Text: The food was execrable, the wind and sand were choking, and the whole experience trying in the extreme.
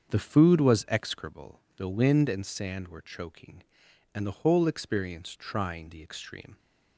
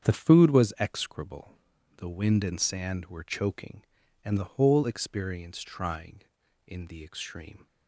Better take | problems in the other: second | starts louder than the rest; until 1.1 s; 7 dB; strong in the second // skips "in"; at 5.8 s

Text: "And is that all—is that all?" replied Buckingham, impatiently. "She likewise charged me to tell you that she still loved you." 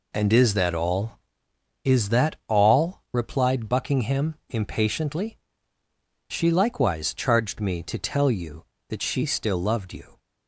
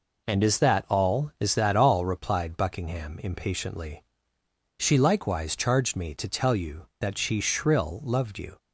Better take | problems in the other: first | says "shrill" for "still"; at 7.4 s

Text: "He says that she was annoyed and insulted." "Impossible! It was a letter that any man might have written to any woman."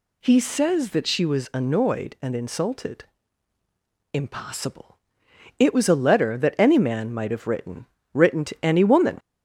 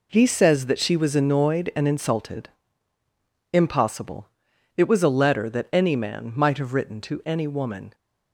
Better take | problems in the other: second | says "written" twice; at 8.1 s

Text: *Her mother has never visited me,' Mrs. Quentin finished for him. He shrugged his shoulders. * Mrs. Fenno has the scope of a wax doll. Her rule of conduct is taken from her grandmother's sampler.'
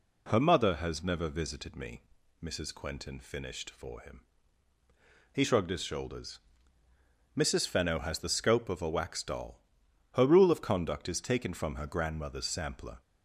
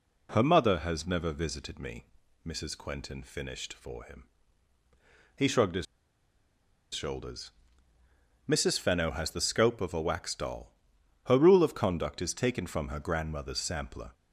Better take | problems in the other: first | pauses between "his" and "shoulders"; at 5.8 s; 1.0 s long

